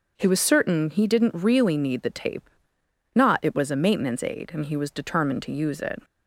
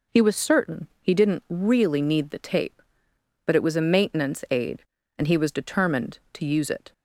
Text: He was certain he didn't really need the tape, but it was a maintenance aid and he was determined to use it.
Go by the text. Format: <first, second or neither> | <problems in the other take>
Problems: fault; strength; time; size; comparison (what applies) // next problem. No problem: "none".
second | says "not" for "but"; at 3.1 s